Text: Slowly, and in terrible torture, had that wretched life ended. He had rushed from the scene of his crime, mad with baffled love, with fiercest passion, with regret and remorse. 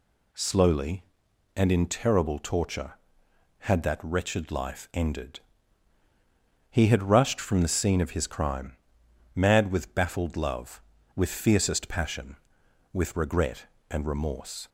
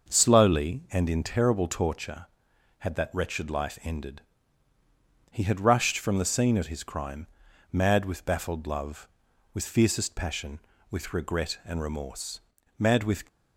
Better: first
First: none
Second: starts louder than the rest; noticeable; until 1.1 s; 6 dB // goes on to say "Mad with"; slight; from 12.7 s on; 0.46 s long

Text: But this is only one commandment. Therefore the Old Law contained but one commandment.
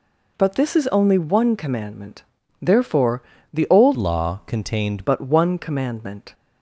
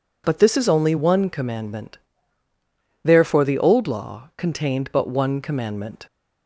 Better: second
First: pauses between "Therefore" and "the"; slight; at 3.2 s; 0.30 s long // changes voice from "Law" to "contained"; from 3.9 to 5.0 s; 1.1 s long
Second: none

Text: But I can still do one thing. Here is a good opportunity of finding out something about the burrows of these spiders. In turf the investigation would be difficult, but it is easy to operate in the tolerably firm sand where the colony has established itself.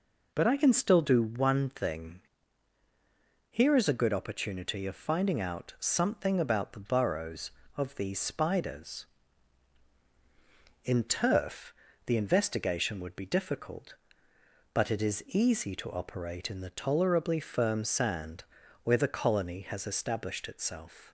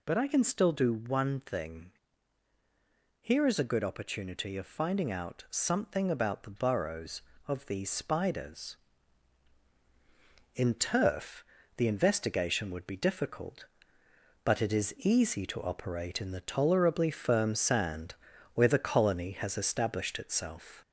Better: first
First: pauses between "turf" and "the"; slight; at 11.7 s; 0.32 s long // pauses between "sand" and "where"; at 18.4 s; 0.40 s long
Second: gets louder; slight; throughout; 2.5 dB // pauses between "turf" and "the"; slight; at 11.4 s; 0.32 s long // pauses between "sand" and "where"; at 18.1 s; 0.40 s long

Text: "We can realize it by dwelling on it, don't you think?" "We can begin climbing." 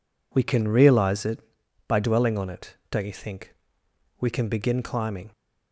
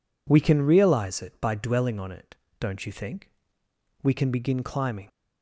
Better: neither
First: none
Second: none

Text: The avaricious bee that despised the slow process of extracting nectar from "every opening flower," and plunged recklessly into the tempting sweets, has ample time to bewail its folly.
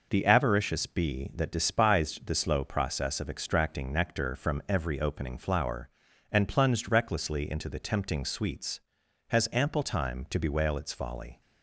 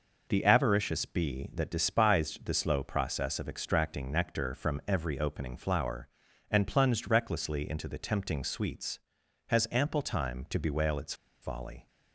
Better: first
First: none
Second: pauses between "its" and "folly"; slight; at 11.1 s; 0.28 s long

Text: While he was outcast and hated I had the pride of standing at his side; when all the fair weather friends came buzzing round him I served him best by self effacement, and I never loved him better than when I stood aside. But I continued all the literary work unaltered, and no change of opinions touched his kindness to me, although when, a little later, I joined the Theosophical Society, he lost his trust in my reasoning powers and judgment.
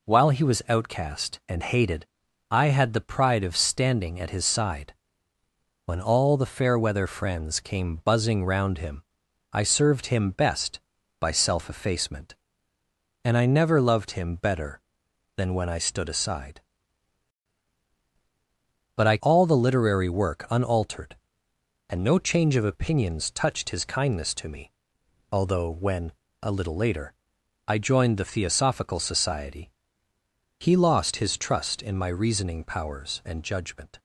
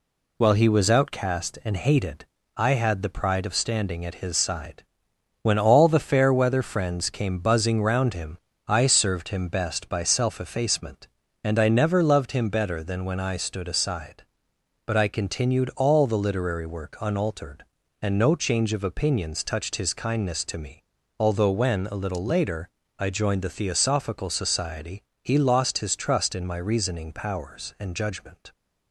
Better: second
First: pauses between "hated" and "I"; at 2.0 s; 0.42 s long // pauses between "him" and "I"; noticeable; at 9.0 s; 0.50 s long // skips "continued"; at 19.2 s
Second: pauses between "hated" and "I"; slight; at 2.2 s; 0.28 s long // pauses between "him" and "I"; slight; at 8.3 s; 0.30 s long

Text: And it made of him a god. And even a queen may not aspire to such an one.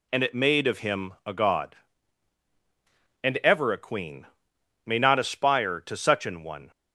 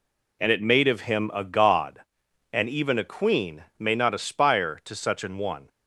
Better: second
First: says "ever" for "even"; at 3.4 s // pauses between "queen" and "may"; noticeable; at 4.2 s; 0.62 s long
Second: none

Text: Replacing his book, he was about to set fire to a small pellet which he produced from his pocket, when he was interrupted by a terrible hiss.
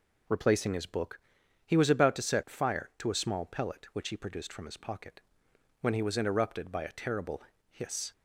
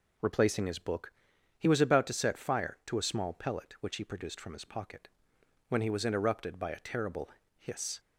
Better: neither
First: pauses between "terrible" and "hiss"; slight; at 7.4 s; 0.28 s long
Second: pauses between "terrible" and "hiss"; slight; at 7.2 s; 0.28 s long

